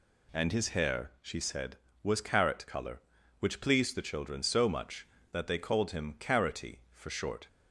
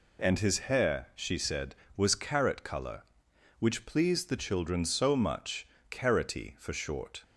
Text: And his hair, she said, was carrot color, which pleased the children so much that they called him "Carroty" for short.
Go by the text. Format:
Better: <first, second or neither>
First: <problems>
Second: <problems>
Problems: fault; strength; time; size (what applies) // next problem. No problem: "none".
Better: first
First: none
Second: skips "that they called him"; at 5.7 s